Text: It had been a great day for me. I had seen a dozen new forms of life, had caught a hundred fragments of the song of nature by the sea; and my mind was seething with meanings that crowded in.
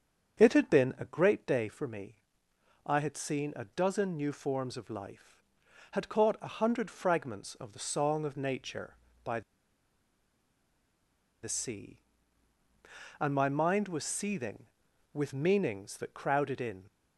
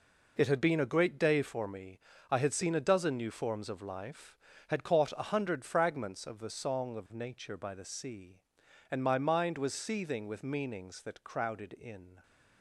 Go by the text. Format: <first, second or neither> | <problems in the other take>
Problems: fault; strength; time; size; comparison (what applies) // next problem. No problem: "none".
second | starts louder than the rest; strong; until 1.4 s; 7 dB // pauses between "by" and "the"; strong; at 9.4 s; 2.0 s long